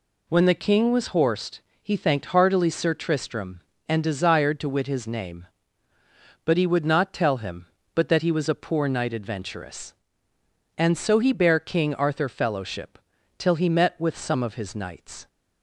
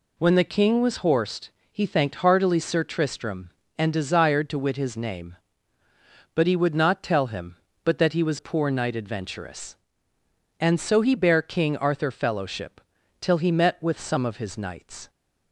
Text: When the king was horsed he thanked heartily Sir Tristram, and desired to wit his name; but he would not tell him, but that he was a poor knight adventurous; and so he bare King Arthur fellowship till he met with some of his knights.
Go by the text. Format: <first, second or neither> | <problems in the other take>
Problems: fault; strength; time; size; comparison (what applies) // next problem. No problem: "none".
first | pauses between "horsed" and "he"; slight; at 1.5 s; 0.20 s long; slight in the first // skips "a"; at 8.3 s // pauses between "fellowship" and "till"; at 12.7 s; 0.40 s long; also in the first